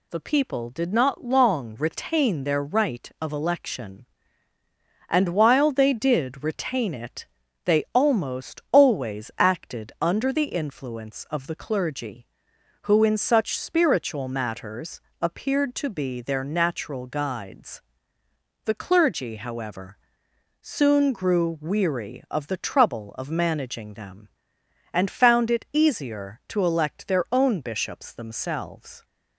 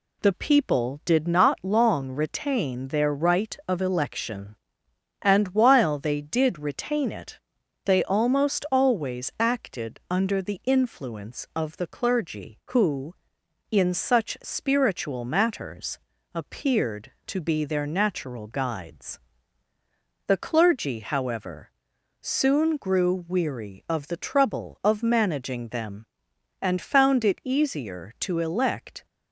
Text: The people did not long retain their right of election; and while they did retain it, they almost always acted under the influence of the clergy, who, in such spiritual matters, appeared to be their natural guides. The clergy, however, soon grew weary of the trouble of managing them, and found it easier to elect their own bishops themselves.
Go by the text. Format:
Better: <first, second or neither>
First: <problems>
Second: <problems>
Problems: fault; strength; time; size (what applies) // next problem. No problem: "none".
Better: first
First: none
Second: stops before "their own bishops themselves"; at 29.0 s